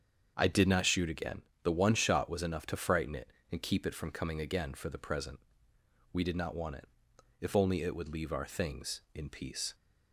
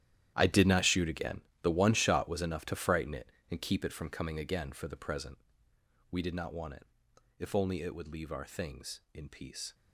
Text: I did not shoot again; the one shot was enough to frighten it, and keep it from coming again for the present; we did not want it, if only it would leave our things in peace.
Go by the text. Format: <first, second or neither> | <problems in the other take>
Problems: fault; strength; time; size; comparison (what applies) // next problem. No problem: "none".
first | gets quieter; strong; throughout; 15 dB // starts louder than the rest; strong; until 1.3 s; 11.5 dB; strong in the first